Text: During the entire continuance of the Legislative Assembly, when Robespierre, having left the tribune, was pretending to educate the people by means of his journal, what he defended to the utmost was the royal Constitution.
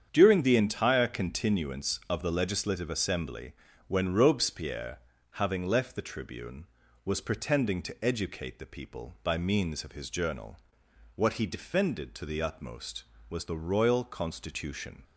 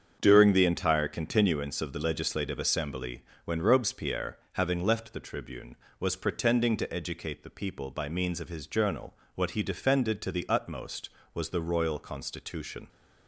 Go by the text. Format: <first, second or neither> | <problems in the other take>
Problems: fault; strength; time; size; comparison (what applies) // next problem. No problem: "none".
neither | starts louder than the rest; strong; the same in both